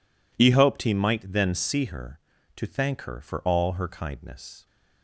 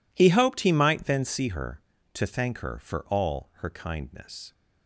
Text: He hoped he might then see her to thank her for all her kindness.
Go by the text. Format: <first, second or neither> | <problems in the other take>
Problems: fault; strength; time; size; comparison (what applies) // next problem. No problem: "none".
neither | none